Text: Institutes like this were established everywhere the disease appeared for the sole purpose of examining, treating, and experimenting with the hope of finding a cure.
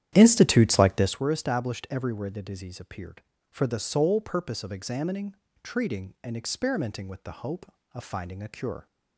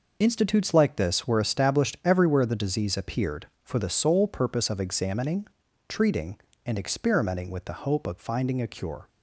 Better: second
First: starts louder than the rest; strong; until 1.3 s; 10.5 dB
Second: none

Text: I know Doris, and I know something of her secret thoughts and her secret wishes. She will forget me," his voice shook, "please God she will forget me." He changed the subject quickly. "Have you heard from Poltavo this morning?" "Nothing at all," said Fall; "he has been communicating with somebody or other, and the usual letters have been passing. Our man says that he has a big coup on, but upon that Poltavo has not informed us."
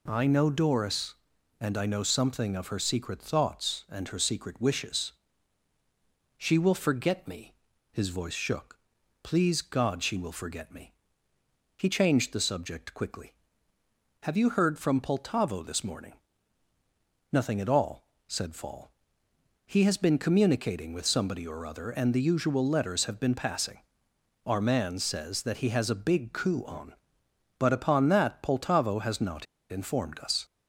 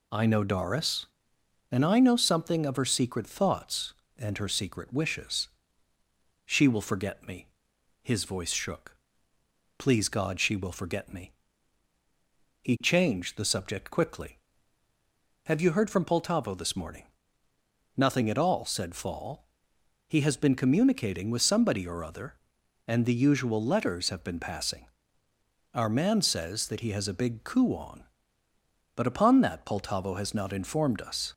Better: second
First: pauses between "not" and "informed"; slight; at 29.4 s; 0.25 s long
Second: none

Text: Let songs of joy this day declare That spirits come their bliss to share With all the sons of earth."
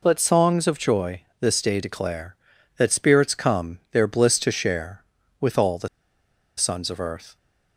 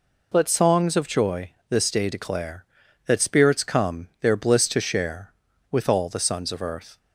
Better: second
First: pauses between "joy" and "this"; slight; at 1.2 s; 0.18 s long // pauses between "the" and "sons"; noticeable; at 5.8 s; 0.69 s long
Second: pauses between "joy" and "this"; slight; at 1.5 s; 0.18 s long

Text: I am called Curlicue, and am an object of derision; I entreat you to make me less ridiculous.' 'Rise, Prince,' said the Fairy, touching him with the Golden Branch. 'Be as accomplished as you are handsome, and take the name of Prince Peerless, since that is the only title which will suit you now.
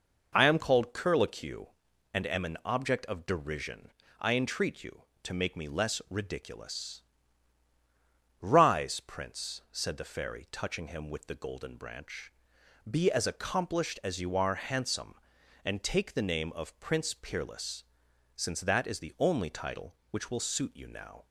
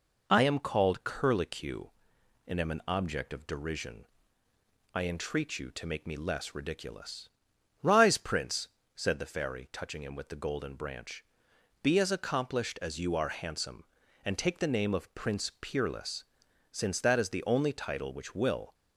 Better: first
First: none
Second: stops before "suit you now"; at 18.7 s

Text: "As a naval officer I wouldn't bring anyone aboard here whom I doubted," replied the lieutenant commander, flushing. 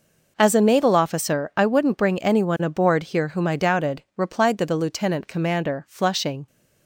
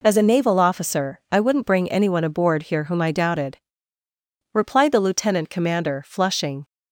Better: second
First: says "the" twice; at 4.6 s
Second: none

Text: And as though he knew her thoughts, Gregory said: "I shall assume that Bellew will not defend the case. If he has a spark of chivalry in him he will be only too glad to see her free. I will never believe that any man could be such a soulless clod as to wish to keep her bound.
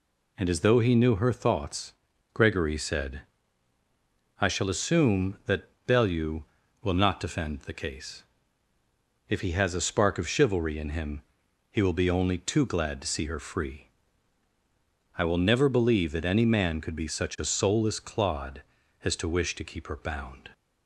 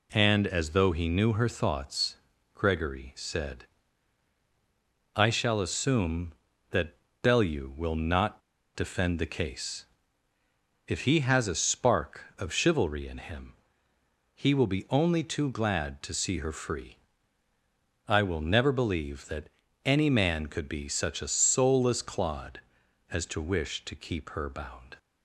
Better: first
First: pauses between "that" and "Bellew"; slight; at 5.6 s; 0.18 s long // pauses between "him" and "he"; noticeable; at 11.2 s; 0.50 s long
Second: pauses between "that" and "Bellew"; slight; at 6.9 s; 0.26 s long // pauses between "not" and "defend"; slight; at 8.4 s; 0.34 s long // pauses between "him" and "he"; noticeable; at 13.5 s; 0.82 s long // pauses between "that" and "any"; slight; at 19.4 s; 0.36 s long

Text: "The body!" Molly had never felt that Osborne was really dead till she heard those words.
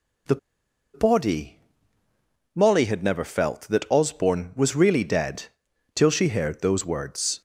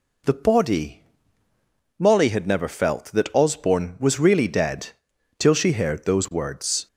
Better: second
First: pauses between "The" and "body"; noticeable; at 0.3 s; 0.58 s long // pauses between "dead" and "till"; noticeable; at 5.4 s; 0.50 s long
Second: pauses between "dead" and "till"; noticeable; at 4.8 s; 0.50 s long

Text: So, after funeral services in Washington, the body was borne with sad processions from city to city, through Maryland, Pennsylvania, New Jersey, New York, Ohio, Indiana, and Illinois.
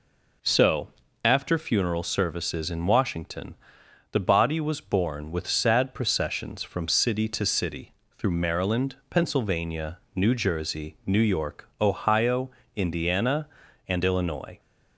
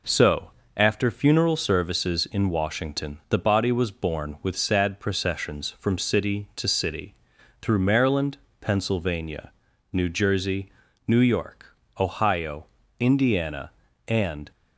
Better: first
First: none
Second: stops before "Illinois"; at 14.5 s

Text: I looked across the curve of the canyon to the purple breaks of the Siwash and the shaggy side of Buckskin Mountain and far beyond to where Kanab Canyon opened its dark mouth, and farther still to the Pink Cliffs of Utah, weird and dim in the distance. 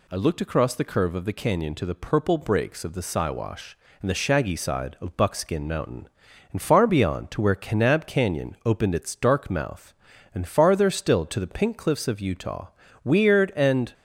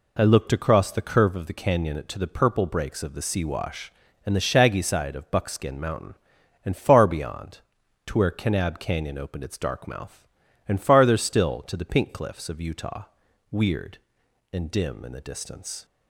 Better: second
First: stops before "dim in the distance"; at 13.9 s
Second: none

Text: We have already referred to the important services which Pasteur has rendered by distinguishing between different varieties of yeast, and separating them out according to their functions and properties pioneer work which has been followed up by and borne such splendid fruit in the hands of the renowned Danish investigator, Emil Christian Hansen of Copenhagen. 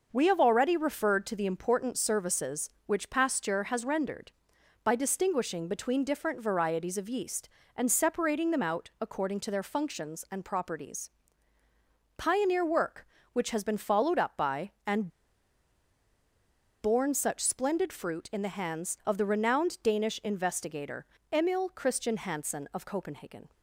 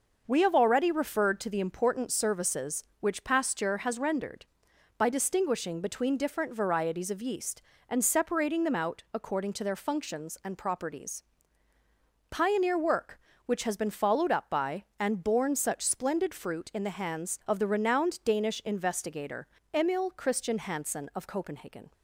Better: second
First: pauses between "properties" and "pioneer"; at 11.0 s; 1.0 s long // pauses between "and" and "borne"; strong; at 15.1 s; 1.7 s long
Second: pauses between "properties" and "pioneer"; at 11.2 s; 1.0 s long

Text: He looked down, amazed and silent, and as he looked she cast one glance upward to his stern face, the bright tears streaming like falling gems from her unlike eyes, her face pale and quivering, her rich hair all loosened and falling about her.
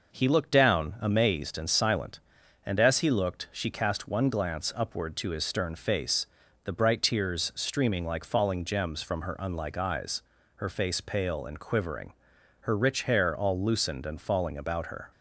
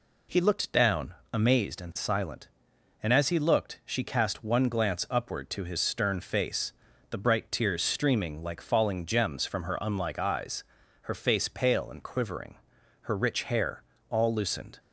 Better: first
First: none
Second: pauses between "hair" and "all"; slight; at 13.8 s; 0.26 s long // stops before "and falling about her"; at 14.7 s

